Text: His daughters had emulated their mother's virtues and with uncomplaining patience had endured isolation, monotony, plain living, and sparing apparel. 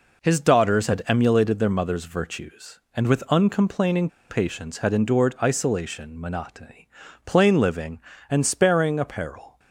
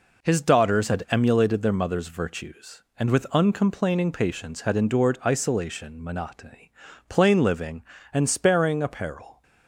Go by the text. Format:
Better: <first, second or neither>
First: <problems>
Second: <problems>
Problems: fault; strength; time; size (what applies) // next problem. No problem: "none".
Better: second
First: pauses between "uncomplaining" and "patience"; slight; at 4.0 s; 0.20 s long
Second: none